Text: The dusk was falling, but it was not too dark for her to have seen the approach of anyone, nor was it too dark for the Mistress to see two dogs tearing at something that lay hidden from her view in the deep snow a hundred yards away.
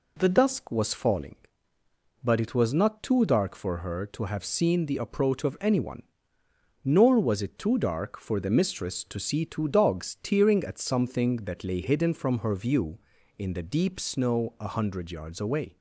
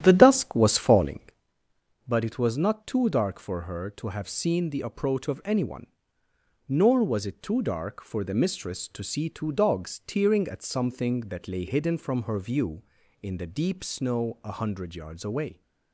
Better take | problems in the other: first | starts louder than the rest; strong; until 1.5 s; 10.5 dB

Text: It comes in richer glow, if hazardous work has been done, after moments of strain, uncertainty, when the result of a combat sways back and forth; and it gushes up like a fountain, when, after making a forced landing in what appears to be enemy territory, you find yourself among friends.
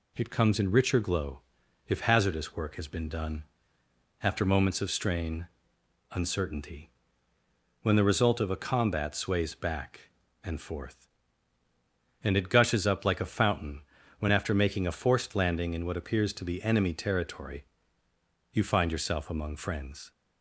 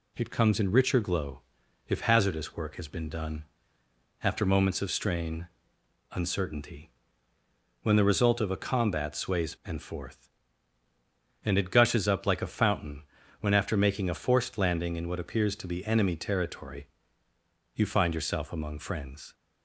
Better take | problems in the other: first | skips "back"; at 9.5 s

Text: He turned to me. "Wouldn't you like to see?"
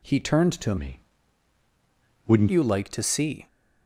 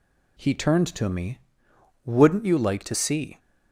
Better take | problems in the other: second | changes voice from "me" to "Wouldn't"; from 0.7 to 2.4 s; 1.7 s long

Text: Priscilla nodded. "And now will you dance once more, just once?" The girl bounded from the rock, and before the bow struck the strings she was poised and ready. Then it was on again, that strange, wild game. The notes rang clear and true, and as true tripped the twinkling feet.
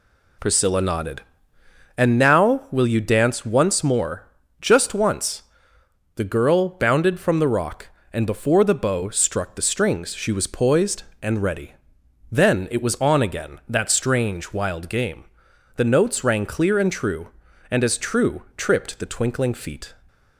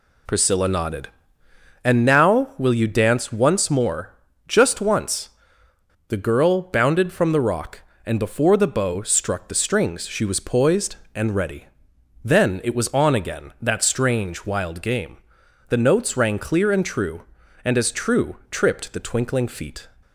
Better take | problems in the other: neither | none

